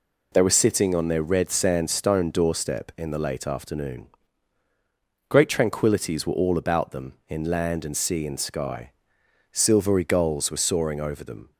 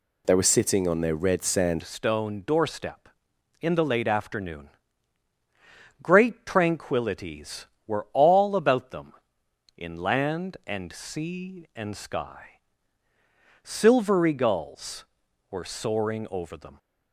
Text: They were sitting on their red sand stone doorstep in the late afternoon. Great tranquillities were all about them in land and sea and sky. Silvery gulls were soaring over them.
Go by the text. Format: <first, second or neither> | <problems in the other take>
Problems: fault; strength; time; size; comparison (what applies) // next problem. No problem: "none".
first | changes voice at "stone"; from 1.8 s on; 14.9 s long